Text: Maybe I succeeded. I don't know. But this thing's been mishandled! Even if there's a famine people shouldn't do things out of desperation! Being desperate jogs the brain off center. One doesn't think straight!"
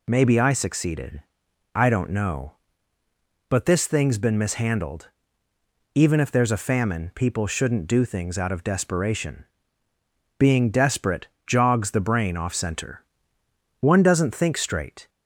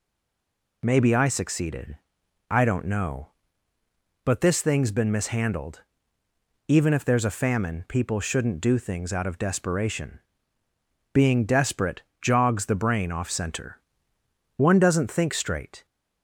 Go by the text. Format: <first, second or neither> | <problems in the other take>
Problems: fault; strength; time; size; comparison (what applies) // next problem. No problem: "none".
first | stays silent before the first word; slight; until 0.8 s; 0.8 s long // pauses between "desperate" and "jogs"; slight; at 12.0 s; 0.20 s long; slight in the first